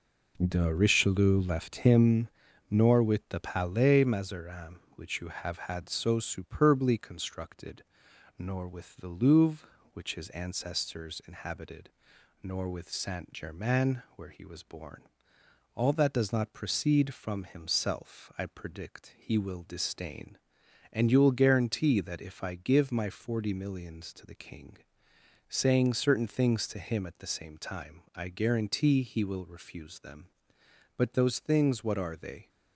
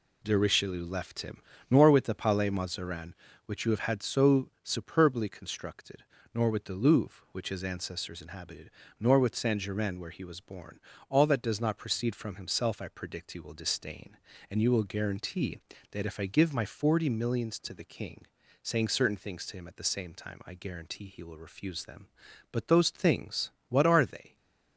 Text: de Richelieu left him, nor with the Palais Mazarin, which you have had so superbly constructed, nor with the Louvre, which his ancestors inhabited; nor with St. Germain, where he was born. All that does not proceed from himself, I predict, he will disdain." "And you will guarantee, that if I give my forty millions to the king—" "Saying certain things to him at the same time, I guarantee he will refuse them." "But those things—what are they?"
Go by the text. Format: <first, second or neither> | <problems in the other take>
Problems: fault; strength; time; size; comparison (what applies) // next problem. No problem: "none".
neither | none